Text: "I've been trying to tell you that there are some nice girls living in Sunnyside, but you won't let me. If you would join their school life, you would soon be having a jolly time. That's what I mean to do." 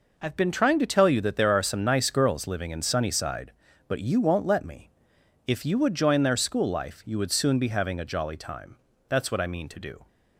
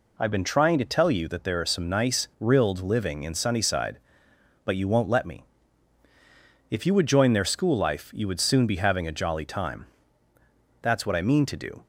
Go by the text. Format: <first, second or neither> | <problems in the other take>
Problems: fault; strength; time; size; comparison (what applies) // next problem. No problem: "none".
first | says "rilled" for "girls"; at 2.3 s